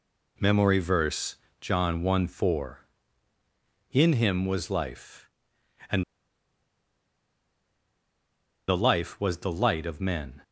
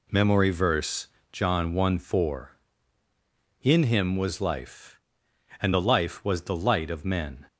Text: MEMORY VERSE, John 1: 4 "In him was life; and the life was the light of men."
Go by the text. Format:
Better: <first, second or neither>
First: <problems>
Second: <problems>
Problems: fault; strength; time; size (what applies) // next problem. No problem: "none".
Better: second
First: pauses between "and" and "the"; strong; at 6.0 s; 2.6 s long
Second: none